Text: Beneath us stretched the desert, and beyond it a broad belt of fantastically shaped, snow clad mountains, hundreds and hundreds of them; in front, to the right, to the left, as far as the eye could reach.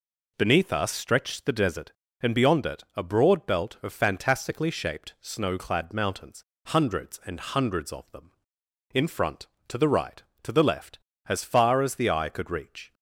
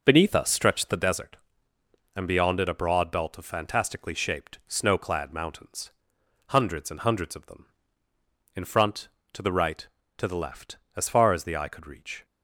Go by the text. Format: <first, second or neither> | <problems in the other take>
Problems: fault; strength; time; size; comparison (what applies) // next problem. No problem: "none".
first | starts louder than the rest; noticeable; until 1.1 s; 5.5 dB